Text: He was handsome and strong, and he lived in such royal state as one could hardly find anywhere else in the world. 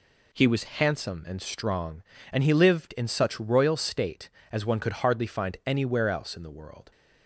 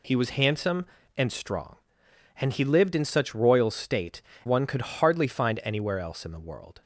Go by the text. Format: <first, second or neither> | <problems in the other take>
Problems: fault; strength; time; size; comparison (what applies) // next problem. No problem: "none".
first | skips "as"; at 4.3 s